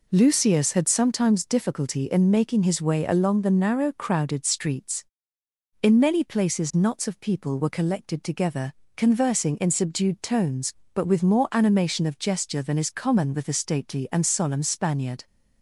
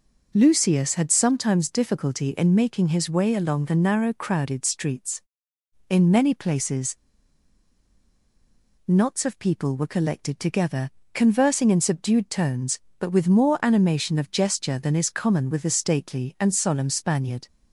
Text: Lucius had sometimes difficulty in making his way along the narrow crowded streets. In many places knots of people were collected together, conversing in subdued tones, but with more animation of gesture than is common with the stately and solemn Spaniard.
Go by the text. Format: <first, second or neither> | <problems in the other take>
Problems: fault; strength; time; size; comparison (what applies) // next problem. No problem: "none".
first | pauses between "places" and "knots"; strong; at 6.9 s; 1.8 s long